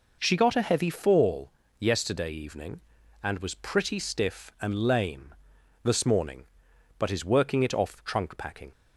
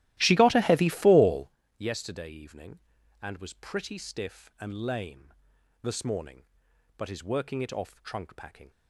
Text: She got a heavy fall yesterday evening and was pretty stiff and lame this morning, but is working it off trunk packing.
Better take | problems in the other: first | starts louder than the rest; strong; until 1.6 s; 15 dB // pauses between "fall" and "yesterday"; slight; at 1.4 s; 0.30 s long; slight in the first // pauses between "lame" and "this"; noticeable; at 5.3 s; 0.50 s long; noticeable in the first

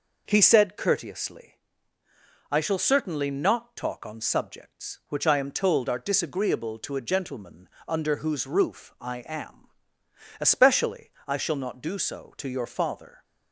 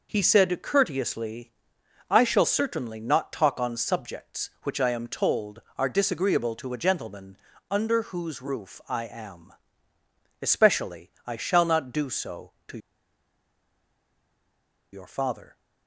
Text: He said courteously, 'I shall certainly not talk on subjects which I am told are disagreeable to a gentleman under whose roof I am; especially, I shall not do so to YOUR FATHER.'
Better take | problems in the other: first | pauses between "gentleman" and "under"; slight; at 7.3 s; 0.32 s long; slight in the first // pauses between "to" and "YOUR"; strong; at 12.7 s; 2.1 s long

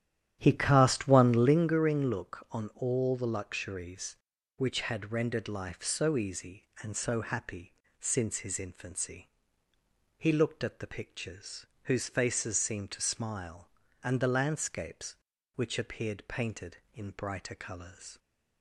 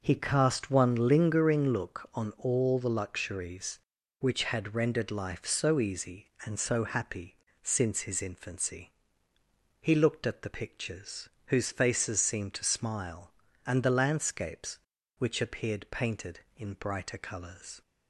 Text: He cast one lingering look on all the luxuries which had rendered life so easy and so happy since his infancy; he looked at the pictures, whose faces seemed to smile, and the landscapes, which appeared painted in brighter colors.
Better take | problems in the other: second | starts louder than the rest; strong; until 1.6 s; 11 dB // pauses between "happy" and "since"; slight; at 7.7 s; 0.26 s long; slight in the second

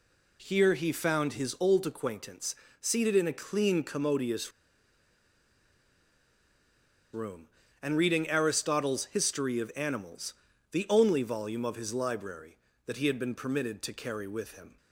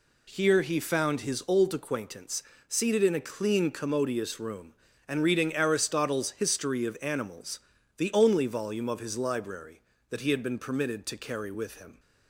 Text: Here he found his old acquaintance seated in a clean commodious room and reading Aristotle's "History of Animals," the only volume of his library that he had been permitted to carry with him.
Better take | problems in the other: second | pauses between "acquaintance" and "seated"; slight; at 2.5 s; 0.26 s long; slight in the second // pauses between "commodious" and "room"; strong; at 4.5 s; 2.6 s long

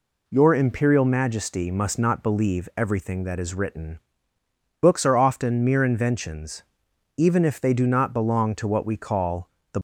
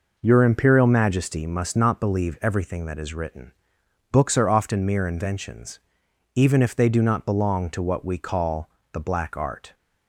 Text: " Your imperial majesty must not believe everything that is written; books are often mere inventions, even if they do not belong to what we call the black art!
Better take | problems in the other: second | pauses between "call" and "the"; slight; at 9.4 s; 0.22 s long; slight in the second // stops before "black art"; at 9.7 s

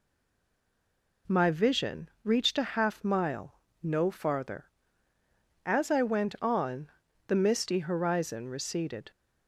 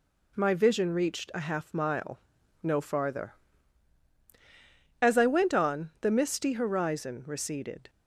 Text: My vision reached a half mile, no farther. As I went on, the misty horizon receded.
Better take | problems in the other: second | stays silent before the first word; noticeable; until 1.2 s; 1.2 s long

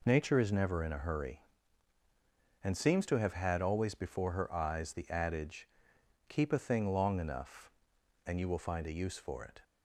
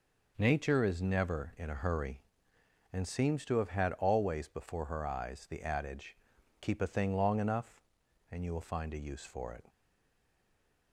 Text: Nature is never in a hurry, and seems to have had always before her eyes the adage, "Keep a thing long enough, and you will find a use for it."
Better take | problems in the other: first | stays silent after the last word; noticeable; from 9.6 s on; 1.3 s long

